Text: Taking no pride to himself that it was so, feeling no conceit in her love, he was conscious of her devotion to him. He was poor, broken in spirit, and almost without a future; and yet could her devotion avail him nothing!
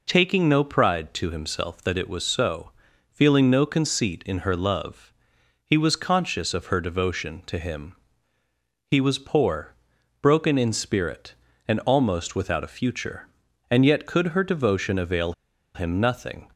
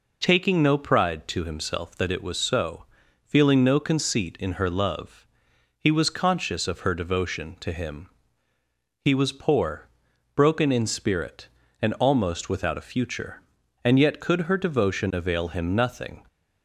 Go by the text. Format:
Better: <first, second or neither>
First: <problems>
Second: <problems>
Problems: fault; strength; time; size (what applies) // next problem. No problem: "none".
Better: second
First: pauses between "avail" and "him"; at 15.3 s; 0.42 s long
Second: none